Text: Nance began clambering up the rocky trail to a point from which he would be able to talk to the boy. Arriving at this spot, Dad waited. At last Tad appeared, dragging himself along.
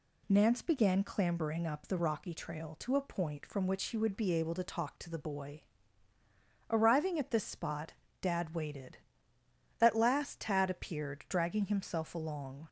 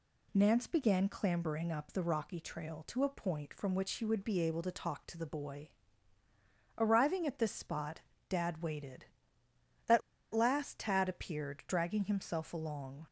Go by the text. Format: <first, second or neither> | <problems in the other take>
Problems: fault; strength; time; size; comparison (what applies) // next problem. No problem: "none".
first | pauses between "At" and "last"; slight; at 10.0 s; 0.33 s long